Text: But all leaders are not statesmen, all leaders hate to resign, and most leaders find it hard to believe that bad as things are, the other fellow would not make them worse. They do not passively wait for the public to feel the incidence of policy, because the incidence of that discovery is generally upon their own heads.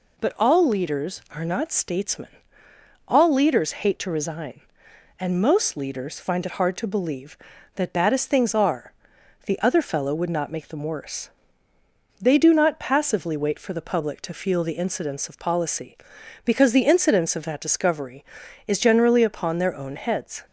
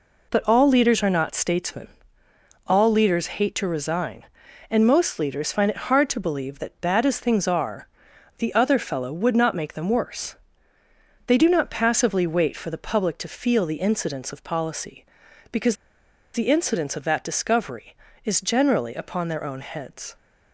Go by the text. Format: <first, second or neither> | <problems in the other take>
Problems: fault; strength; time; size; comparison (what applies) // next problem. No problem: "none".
first | pauses between "because" and "the"; noticeable; at 15.7 s; 0.59 s long